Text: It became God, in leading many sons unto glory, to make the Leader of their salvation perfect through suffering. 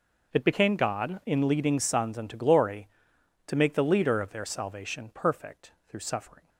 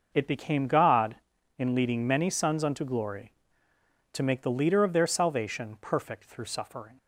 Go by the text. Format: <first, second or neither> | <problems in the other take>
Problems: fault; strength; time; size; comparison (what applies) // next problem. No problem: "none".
second | skips "many"; at 1.7 s // pauses between "perfect" and "through"; slight; at 5.7 s; 0.16 s long